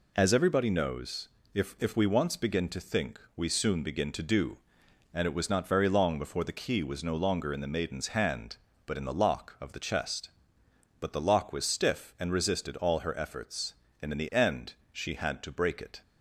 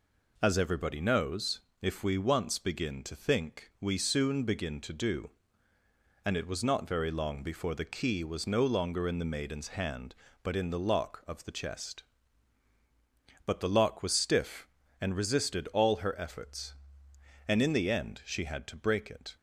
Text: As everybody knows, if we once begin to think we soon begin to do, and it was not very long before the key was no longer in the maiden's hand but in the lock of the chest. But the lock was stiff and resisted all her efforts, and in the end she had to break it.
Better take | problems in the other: second | says "if" twice; at 1.8 s // pauses between "think" and "we"; slight; at 3.1 s; 0.16 s long // pauses between "end" and "she"; slight; at 14.7 s; 0.18 s long

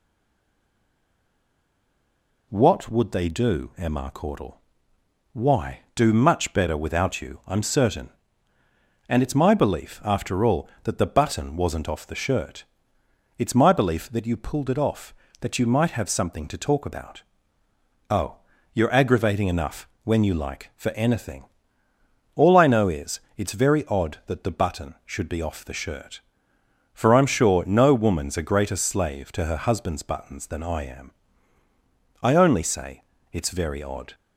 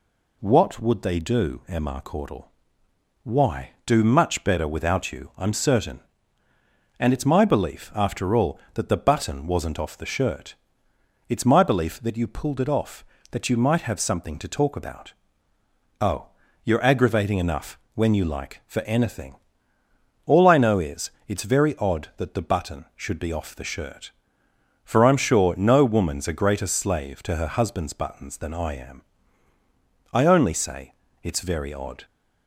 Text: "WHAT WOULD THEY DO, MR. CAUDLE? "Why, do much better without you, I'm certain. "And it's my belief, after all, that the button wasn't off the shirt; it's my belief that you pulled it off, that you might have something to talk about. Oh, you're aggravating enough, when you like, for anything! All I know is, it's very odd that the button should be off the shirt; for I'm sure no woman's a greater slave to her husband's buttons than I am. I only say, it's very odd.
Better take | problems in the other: second | stays silent before the first word; until 2.5 s; 2.5 s long

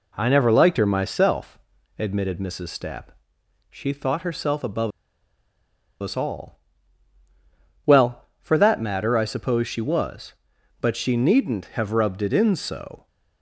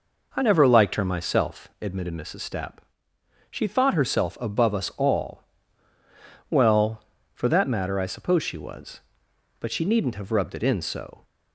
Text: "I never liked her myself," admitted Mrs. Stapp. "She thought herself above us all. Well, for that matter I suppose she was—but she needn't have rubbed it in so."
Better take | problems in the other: second | pauses between "above" and "us"; at 4.9 s; 1.1 s long

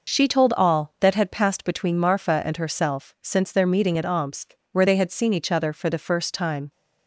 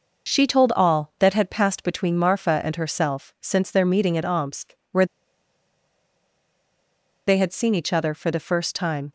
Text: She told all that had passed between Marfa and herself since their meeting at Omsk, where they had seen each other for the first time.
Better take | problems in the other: first | pauses between "where" and "they"; strong; at 5.0 s; 2.2 s long

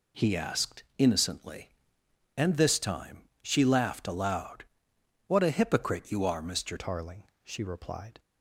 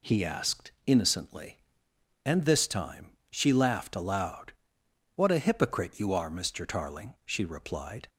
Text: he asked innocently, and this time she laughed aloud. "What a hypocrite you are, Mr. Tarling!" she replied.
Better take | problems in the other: second | pauses between "asked" and "innocently"; slight; at 0.8 s; 0.16 s long; slight in the second // pauses between "time" and "she"; slight; at 3.2 s; 0.18 s long; slight in the second // changes voice at "Tarling"; from 6.7 s on; 1.4 s long

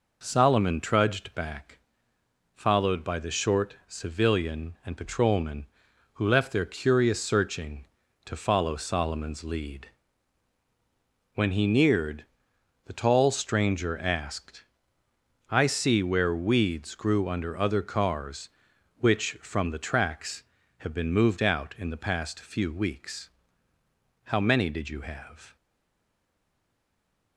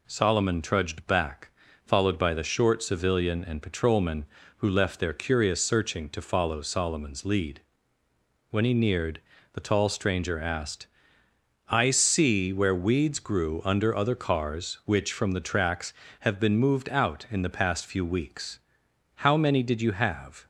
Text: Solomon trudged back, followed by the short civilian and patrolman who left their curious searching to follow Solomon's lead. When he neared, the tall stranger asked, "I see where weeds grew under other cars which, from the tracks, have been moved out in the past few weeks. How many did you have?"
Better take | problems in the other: second | stays silent after the last word; noticeable; from 25.5 s on; 1.8 s long

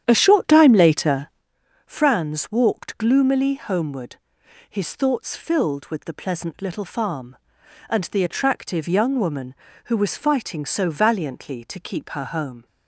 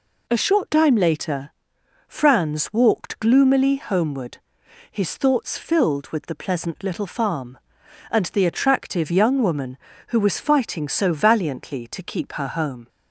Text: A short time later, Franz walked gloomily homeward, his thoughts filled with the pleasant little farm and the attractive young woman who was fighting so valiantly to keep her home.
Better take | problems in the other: second | starts louder than the rest; strong; until 1.5 s; 9.5 dB

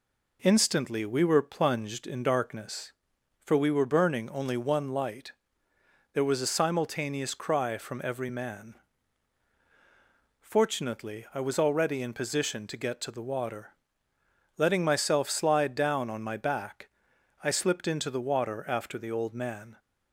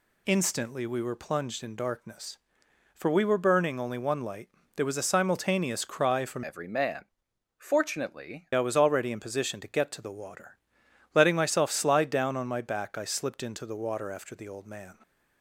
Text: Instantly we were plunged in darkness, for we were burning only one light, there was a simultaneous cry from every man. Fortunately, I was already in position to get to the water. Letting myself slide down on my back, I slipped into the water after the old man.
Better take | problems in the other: first | changes voice from "every" to "Fortunately"; from 6.4 to 8.4 s; 2.0 s long

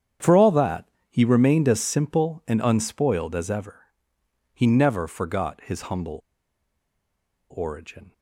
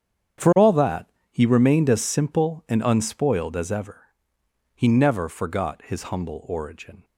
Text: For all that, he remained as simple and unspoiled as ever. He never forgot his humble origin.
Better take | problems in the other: second | starts louder than the rest; strong; until 1.4 s; 8.5 dB; strong in the second // pauses between "humble" and "origin"; strong; at 6.2 s; 1.3 s long

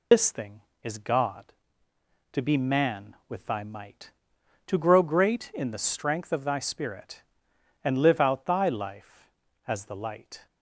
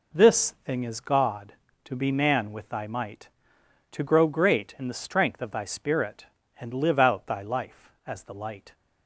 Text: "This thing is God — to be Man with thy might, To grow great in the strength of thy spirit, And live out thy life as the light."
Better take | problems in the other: second | loses the start of "This"; at 0.1 s; 115 ms

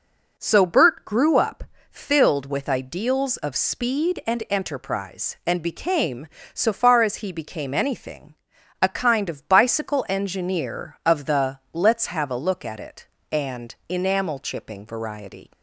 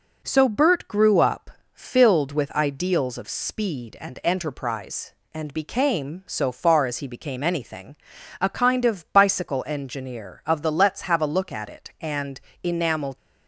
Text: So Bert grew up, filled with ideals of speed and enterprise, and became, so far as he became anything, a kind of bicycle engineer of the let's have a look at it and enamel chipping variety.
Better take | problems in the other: first | pauses between "and" and "enamel"; slight; at 12.3 s; 0.24 s long // stops before "chipping variety"; at 13.1 s

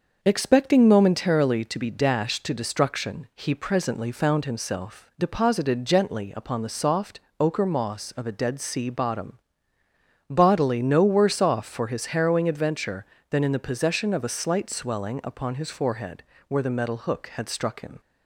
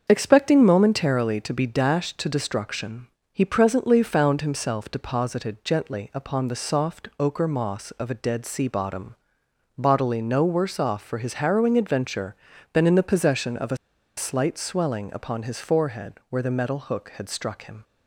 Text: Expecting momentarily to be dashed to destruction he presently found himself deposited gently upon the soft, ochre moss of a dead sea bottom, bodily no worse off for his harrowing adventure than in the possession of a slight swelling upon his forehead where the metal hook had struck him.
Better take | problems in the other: first | starts louder than the rest; until 1.1 s; 7 dB; also in the first // pauses between "destruction" and "he"; slight; at 3.0 s; 0.26 s long // pauses between "a" and "slight"; at 13.7 s; 0.40 s long // pauses between "forehead" and "where"; slight; at 16.1 s; 0.18 s long; slight in the first

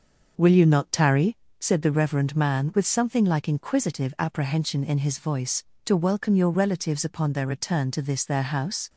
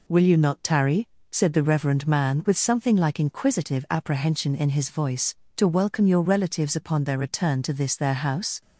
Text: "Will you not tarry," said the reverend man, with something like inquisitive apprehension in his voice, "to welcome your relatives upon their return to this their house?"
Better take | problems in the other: second | starts louder than the rest; until 1.4 s; 6 dB

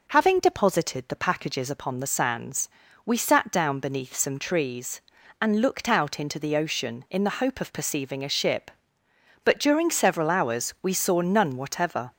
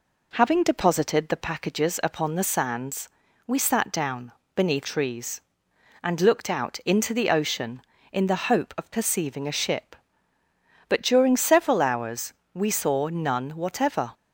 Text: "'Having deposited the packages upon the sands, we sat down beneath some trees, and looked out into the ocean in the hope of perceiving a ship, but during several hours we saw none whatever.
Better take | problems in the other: first | pauses between "down" and "beneath"; slight; at 4.3 s; 0.24 s long // skips "some"; at 4.8 s // pauses between "hours" and "we"; slight; at 12.3 s; 0.18 s long

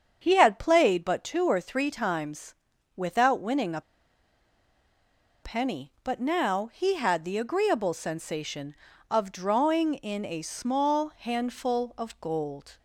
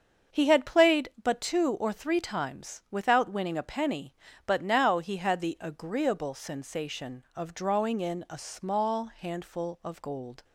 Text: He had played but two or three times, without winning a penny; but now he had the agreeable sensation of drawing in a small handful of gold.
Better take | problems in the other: second | starts louder than the rest; strong; until 1.2 s; 7.5 dB; also in the second // pauses between "a" and "penny"; strong; at 3.8 s; 1.6 s long

